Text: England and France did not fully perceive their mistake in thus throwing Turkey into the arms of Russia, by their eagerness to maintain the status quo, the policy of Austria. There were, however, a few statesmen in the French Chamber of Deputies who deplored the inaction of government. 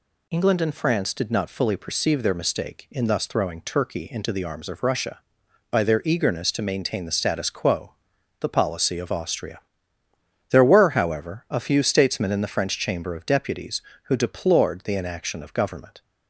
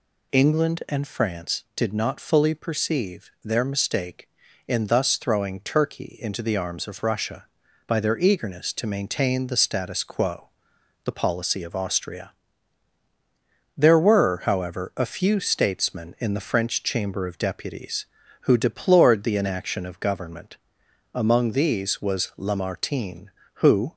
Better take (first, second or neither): first